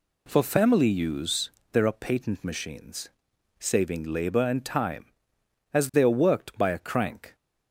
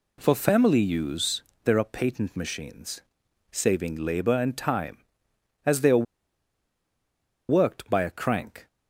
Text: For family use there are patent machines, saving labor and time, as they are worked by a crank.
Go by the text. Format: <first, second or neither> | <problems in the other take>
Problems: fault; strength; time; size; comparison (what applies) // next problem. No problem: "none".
first | pauses between "use" and "there"; slight; at 1.4 s; 0.20 s long; slight in the first // pauses between "are" and "worked"; strong; at 6.0 s; 1.4 s long